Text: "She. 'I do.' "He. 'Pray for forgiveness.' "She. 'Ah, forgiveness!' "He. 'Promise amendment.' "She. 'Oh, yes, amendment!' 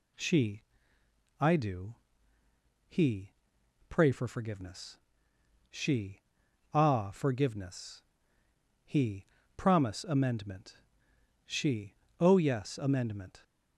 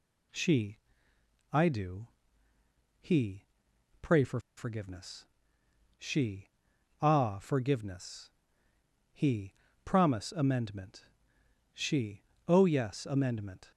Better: first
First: none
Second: pauses between "for" and "forgiveness"; slight; at 4.3 s; 0.17 s long

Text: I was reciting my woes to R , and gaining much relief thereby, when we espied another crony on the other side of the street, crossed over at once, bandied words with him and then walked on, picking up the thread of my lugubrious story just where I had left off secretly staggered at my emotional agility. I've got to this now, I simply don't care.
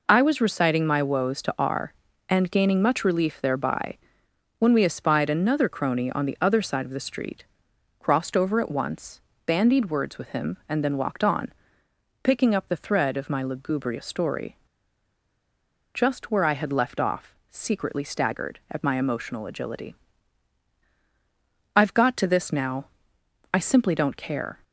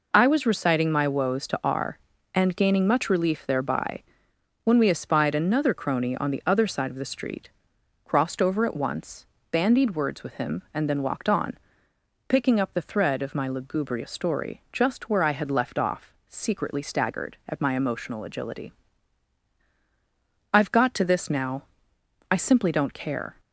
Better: second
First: pauses between "story" and "just"; strong; at 14.5 s; 1.3 s long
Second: none

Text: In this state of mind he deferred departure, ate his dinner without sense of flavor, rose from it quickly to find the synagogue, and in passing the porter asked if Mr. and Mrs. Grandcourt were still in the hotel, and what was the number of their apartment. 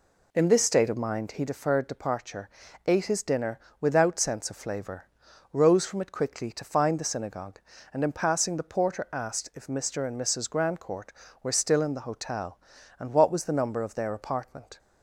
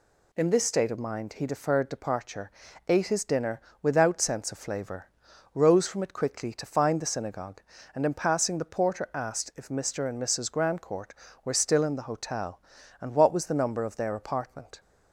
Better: second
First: starts louder than the rest; slight; until 1.5 s; 2.5 dB // pauses between "dinner" and "without"; slight; at 3.5 s; 0.22 s long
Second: pauses between "dinner" and "without"; slight; at 3.5 s; 0.22 s long

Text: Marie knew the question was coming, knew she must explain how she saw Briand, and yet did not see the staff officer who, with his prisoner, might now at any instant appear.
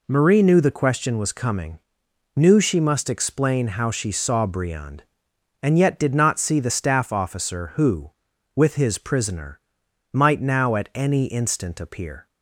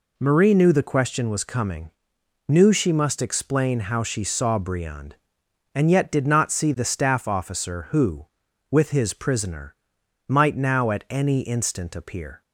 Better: neither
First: none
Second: none

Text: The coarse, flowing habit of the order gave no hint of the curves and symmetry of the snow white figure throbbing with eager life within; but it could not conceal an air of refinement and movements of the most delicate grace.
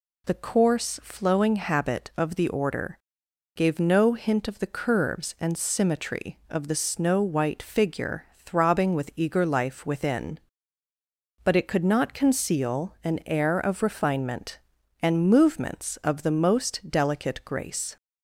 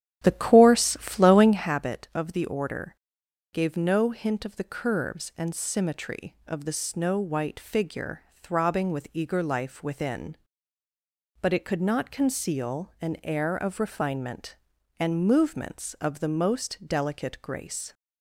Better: first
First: pauses between "order" and "gave"; noticeable; at 2.9 s; 0.58 s long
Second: starts louder than the rest; strong; until 1.7 s; 10.5 dB // pauses between "order" and "gave"; noticeable; at 2.9 s; 0.58 s long

